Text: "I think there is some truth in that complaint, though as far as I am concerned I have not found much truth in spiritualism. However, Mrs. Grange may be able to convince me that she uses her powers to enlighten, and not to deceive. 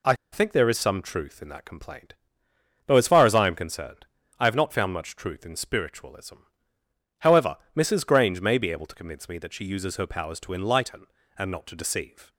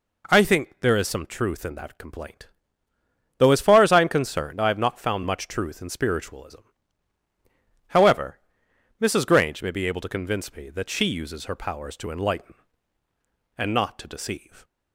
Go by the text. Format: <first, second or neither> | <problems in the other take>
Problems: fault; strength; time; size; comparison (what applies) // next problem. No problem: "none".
second | pauses between "I" and "think"; slight; at 0.1 s; 0.17 s long // pauses between "concerned" and "I"; slight; at 4.0 s; 0.32 s long